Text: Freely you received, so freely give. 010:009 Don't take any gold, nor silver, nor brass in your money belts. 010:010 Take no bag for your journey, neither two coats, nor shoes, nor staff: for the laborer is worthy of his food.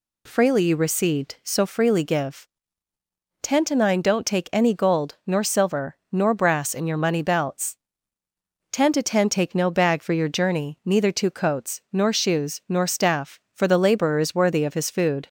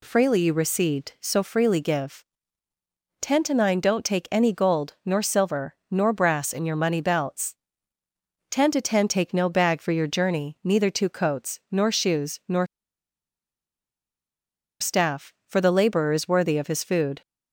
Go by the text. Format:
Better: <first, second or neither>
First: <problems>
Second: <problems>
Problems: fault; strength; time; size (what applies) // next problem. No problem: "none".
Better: first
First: none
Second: pauses between "nor" and "staff"; strong; at 12.6 s; 2.1 s long